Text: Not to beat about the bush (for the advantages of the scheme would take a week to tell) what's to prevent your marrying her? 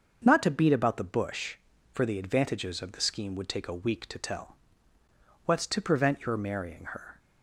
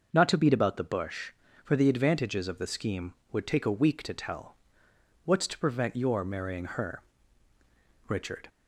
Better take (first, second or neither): first